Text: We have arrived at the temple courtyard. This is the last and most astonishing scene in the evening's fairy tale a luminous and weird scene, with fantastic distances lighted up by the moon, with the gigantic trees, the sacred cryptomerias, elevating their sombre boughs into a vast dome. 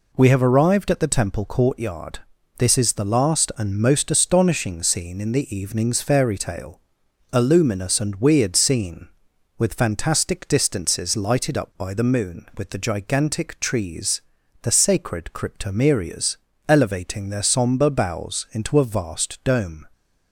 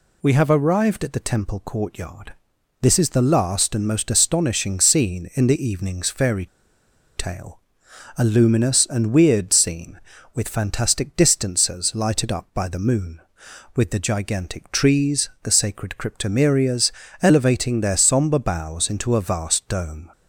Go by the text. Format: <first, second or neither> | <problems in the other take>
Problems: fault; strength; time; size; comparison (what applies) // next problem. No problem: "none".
first | pauses between "fairy" and "tale"; noticeable; at 6.4 s; 0.70 s long // pauses between "tale" and "a"; noticeable; at 7.5 s; 0.60 s long; noticeable in the first